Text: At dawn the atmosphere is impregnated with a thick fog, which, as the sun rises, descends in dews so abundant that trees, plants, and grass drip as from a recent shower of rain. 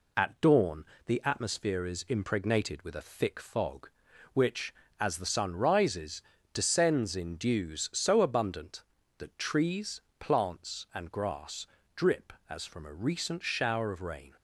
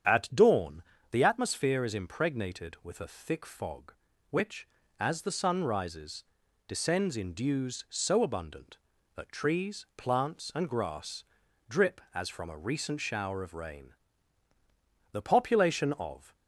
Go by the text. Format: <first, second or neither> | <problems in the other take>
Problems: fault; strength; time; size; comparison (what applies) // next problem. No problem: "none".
first | starts louder than the rest; strong; until 1.3 s; 8.5 dB // pauses between "dawn" and "the"; slight; at 0.8 s; 0.26 s long; slight in the first // pauses between "grass" and "drip"; noticeable; at 11.2 s; 0.46 s long; slight in the first // goes on to say "The population of"; noticeable; from 15.1 s on; 1.2 s long